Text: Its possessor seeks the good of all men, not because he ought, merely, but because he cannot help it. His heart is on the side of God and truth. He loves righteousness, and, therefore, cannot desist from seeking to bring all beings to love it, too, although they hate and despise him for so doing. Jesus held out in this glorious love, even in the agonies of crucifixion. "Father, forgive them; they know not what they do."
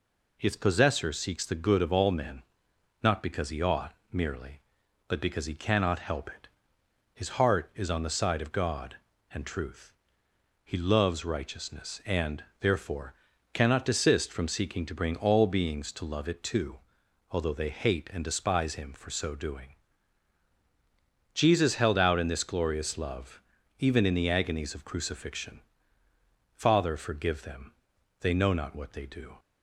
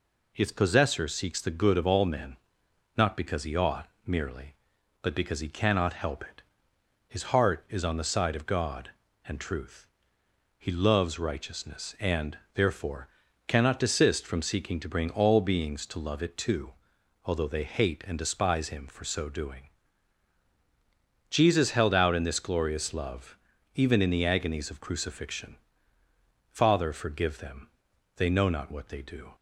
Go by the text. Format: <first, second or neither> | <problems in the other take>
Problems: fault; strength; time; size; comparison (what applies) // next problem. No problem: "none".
neither | none